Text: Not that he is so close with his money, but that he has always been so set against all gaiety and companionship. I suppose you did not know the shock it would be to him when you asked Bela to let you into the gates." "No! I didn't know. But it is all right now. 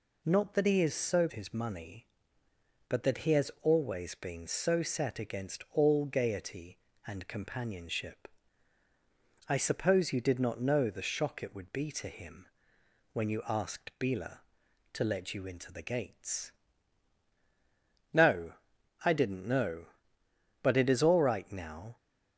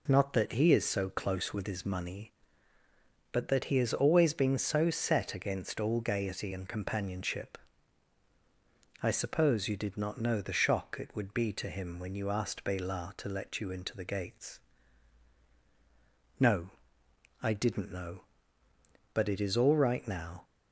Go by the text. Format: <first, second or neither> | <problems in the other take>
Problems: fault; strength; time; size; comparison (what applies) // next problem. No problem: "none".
second | skips "close with"; at 1.2 s // pauses between "him" and "when"; noticeable; at 12.4 s; 0.66 s long